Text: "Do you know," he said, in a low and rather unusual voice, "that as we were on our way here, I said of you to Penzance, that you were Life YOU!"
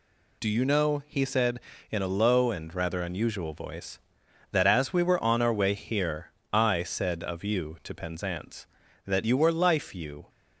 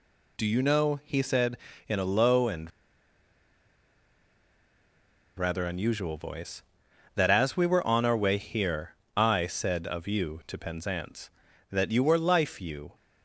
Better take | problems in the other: first | pauses between "and" and "rather"; strong; at 2.7 s; 2.6 s long

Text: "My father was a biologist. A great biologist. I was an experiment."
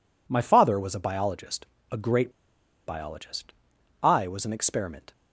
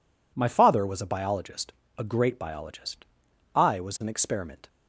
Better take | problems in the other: second | pauses between "great" and "biologist"; noticeable; at 2.3 s; 0.55 s long

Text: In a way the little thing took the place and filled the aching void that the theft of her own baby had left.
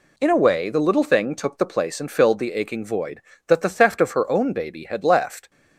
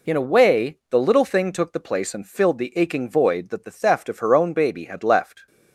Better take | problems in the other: neither | none

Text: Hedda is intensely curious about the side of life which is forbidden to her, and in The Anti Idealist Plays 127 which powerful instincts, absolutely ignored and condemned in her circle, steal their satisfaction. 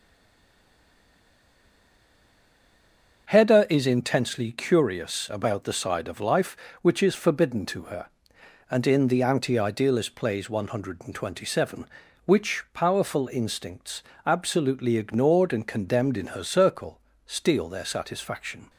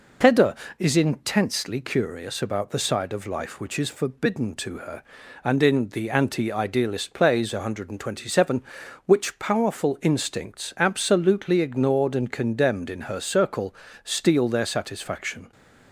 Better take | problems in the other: second | stays silent before the first word; strong; until 3.2 s; 3.2 s long // starts louder than the rest; until 4.3 s; 6.5 dB

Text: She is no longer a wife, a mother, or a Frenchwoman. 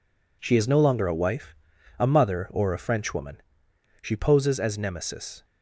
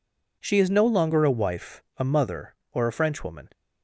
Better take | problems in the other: second | goes on to say "She poses as Nemesis"; from 4.0 s on; 1.4 s long

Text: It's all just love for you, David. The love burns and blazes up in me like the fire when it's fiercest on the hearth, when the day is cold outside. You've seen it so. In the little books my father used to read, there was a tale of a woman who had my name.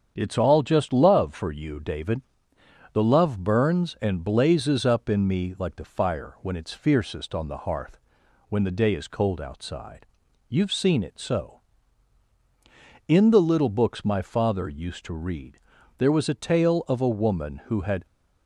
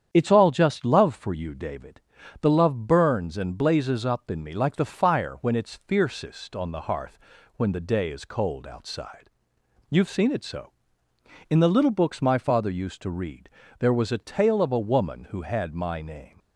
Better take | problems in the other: second | starts louder than the rest; strong; until 1.1 s; 8 dB; strong in the second // stops before "my name"; at 18.0 s

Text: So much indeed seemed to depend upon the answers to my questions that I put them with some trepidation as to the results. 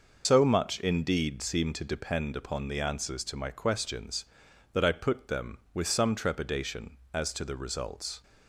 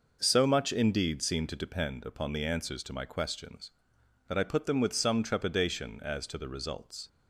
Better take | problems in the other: second | loses the start of "So"; at 0.2 s; 105 ms

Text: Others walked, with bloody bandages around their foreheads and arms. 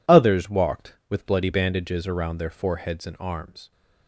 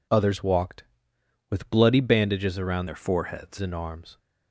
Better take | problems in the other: first | changes voice from "their" to "foreheads"; from 2.8 to 3.5 s; 0.7 s long

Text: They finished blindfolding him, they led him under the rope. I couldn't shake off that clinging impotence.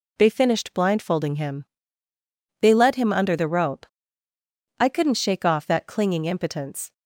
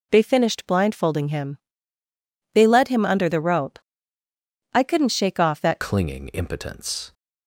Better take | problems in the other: first | changes voice at "clinging"; from 5.8 s on; 1.3 s long

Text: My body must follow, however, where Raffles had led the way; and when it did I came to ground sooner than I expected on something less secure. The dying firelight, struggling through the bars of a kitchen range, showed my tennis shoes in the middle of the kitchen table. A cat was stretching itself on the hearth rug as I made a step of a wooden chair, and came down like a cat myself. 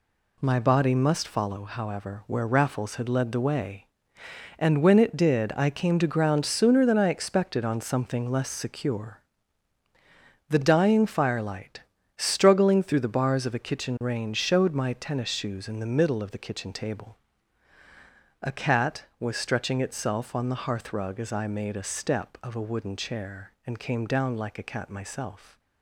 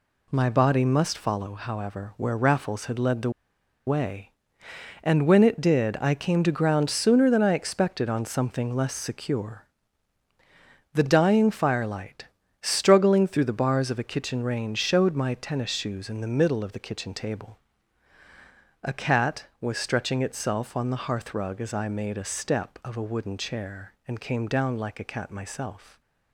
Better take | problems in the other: first | pauses between "the" and "way"; noticeable; at 3.2 s; 0.56 s long

